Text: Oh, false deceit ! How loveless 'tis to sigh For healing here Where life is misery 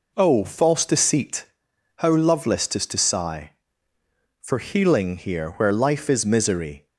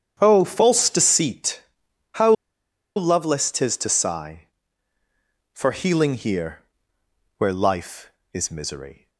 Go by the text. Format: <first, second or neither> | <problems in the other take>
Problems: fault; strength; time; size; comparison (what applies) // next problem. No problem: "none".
first | starts louder than the rest; strong; until 1.2 s; 8.5 dB // pauses between "How" and "loveless"; noticeable; at 2.3 s; 0.64 s long // pauses between "here" and "Where"; noticeable; at 6.6 s; 0.76 s long